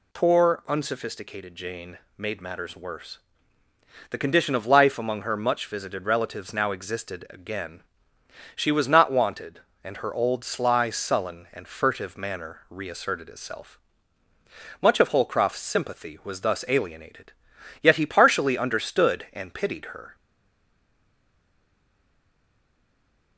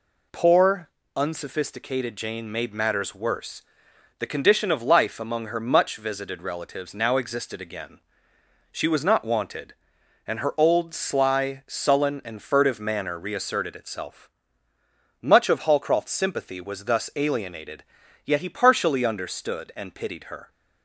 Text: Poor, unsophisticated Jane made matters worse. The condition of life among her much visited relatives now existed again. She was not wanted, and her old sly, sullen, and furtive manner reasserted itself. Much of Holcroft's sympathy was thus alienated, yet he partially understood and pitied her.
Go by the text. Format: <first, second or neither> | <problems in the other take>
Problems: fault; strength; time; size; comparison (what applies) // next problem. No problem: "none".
second | pauses between "Jane" and "made"; slight; at 1.9 s; 0.20 s long // stays silent after the last word; strong; from 20.1 s on; 3.2 s long